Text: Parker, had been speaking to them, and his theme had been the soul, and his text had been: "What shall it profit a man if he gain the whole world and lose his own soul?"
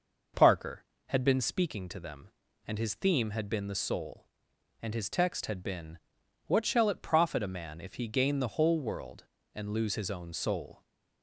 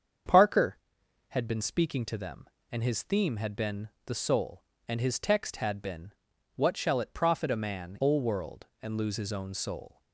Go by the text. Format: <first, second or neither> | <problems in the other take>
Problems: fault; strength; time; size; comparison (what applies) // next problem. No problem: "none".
first | starts louder than the rest; strong; until 1.7 s; 7.5 dB // pauses between "been" and "the"; slight; at 3.8 s; 0.20 s long // skips "if he gain the"; at 8.0 s